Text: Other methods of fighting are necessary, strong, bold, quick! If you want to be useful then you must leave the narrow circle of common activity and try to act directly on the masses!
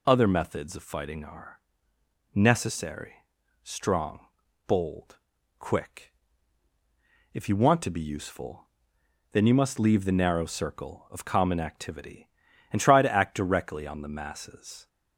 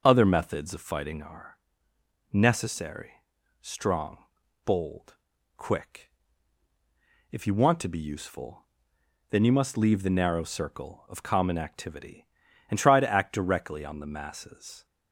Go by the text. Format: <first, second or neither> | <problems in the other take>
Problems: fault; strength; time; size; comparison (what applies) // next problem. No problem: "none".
first | starts louder than the rest; noticeable; until 1.3 s; 6 dB // pauses between "are" and "necessary"; noticeable; at 1.5 s; 0.72 s long; noticeable in the first // pauses between "useful" and "then"; noticeable; at 8.6 s; 0.66 s long; noticeable in the first